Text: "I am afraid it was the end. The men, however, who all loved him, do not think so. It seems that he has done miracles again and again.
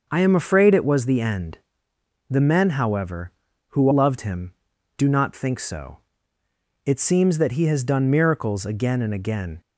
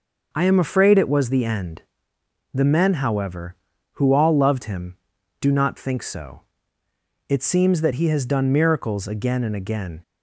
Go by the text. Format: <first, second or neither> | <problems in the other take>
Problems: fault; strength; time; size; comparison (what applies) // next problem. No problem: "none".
second | skips "all"; at 3.9 s